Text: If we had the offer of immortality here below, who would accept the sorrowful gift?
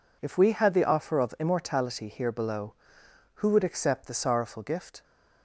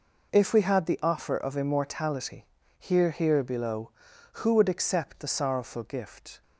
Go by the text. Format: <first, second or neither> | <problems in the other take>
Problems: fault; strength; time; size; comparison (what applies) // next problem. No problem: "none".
first | pauses between "immortality" and "here"; slight; at 2.4 s; 0.34 s long // says "here" twice; at 3.1 s